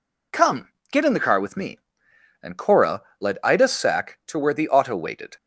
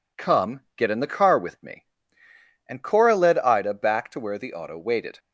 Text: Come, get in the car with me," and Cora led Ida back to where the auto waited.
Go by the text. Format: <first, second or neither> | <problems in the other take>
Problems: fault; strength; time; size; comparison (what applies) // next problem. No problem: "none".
second | pauses between "Cora" and "led"; slight; at 3.0 s; 0.18 s long // says "sack" for "back"; at 3.6 s